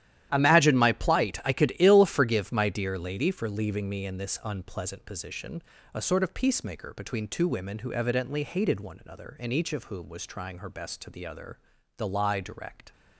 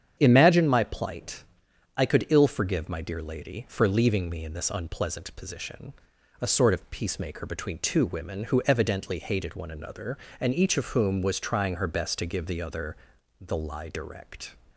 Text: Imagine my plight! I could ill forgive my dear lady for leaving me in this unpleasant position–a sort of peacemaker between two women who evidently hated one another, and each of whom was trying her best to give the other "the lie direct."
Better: second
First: starts louder than the rest; strong; until 1.3 s; 12 dB // skips "give"; at 11.0 s // pauses between "other" and "the"; at 11.5 s; 0.38 s long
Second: starts louder than the rest; strong; until 1.2 s; 8 dB // pauses between "other" and "the"; at 12.9 s; 0.44 s long

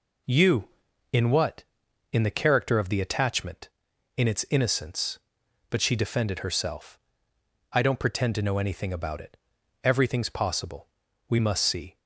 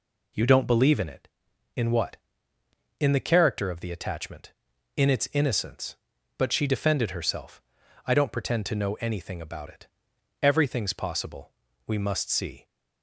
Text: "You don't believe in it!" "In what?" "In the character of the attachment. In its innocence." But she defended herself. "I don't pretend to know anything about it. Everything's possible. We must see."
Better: second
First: skips "don't believe in it"; at 0.9 s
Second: none

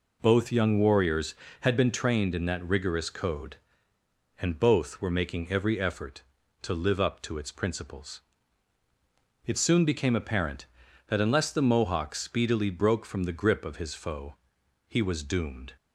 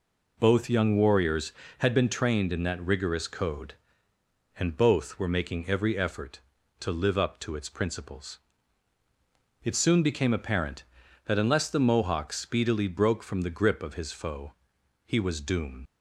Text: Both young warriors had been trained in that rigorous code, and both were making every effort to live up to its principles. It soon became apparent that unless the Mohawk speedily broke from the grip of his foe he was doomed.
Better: first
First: pauses between "foe" and "he"; noticeable; at 14.3 s; 0.54 s long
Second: pauses between "foe" and "he"; noticeable; at 14.5 s; 0.54 s long // leaves "doomed" unfinished; at 15.8 s; 80 ms

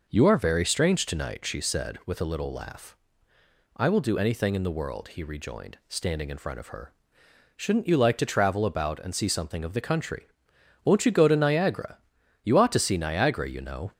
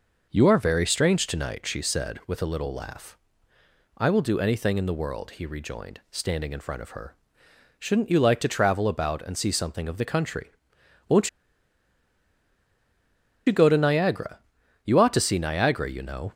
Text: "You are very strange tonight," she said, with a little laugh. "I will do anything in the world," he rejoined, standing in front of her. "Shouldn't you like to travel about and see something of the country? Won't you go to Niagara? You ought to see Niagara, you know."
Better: first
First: none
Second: pauses between "Won't" and "you"; strong; at 11.2 s; 2.1 s long

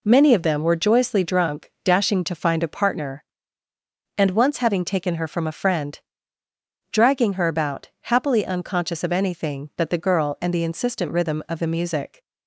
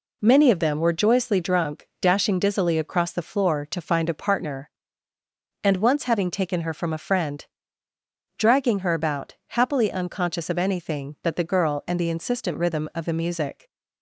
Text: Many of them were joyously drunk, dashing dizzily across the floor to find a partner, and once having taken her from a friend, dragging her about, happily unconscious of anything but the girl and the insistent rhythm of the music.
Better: second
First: skips "dizzily across the floor"; at 2.2 s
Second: none

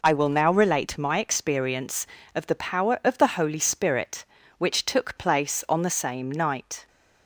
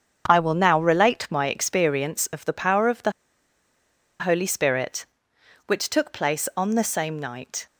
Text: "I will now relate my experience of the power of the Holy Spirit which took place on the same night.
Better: first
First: none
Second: starts louder than the rest; strong; until 1.2 s; 7.5 dB // pauses between "the" and "Holy"; at 3.1 s; 1.0 s long

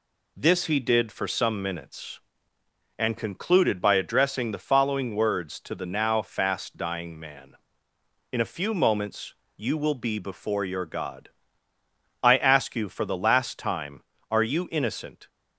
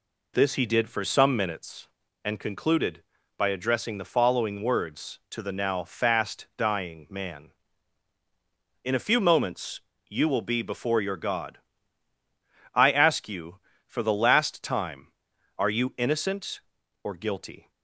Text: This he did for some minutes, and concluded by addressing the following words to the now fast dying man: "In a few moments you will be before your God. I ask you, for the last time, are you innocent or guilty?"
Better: second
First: pauses between "moments" and "you"; slight; at 9.3 s; 0.24 s long // stops before "or guilty"; at 15.2 s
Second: pauses between "moments" and "you"; slight; at 9.7 s; 0.30 s long

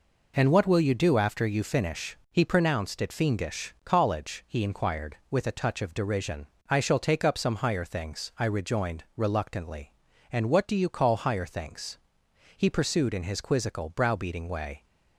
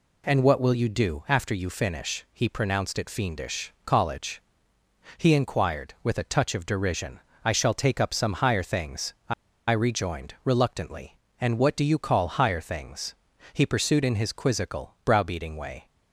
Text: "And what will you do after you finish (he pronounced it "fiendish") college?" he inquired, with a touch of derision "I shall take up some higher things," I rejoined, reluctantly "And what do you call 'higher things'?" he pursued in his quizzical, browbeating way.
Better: first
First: pauses between "derision" and "I"; slight; at 6.4 s; 0.22 s long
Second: pauses between "derision" and "I"; slight; at 7.1 s; 0.26 s long // pauses between "I" and "rejoined"; at 9.3 s; 0.36 s long

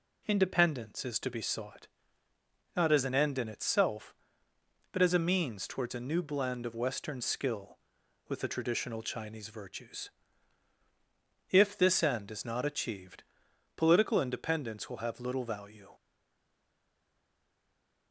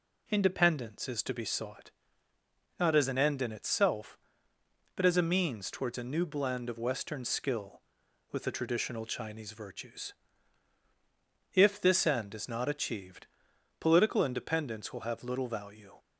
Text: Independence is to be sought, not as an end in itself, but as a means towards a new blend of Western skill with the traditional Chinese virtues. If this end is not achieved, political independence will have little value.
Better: second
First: stays silent after the last word; from 15.9 s on; 2.2 s long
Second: none

